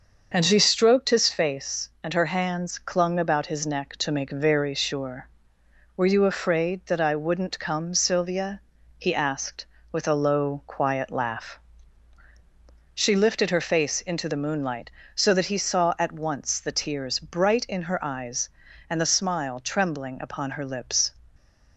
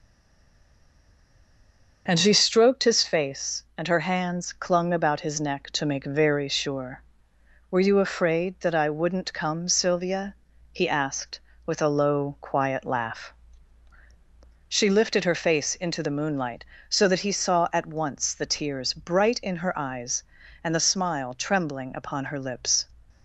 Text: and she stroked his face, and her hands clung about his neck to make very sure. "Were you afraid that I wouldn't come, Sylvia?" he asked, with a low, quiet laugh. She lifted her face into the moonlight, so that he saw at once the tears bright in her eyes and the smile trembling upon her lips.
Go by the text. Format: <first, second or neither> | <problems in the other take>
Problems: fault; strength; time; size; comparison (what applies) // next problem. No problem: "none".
first | stays silent before the first word; noticeable; until 2.0 s; 2.0 s long // starts louder than the rest; until 3.0 s; 6.5 dB; also in the first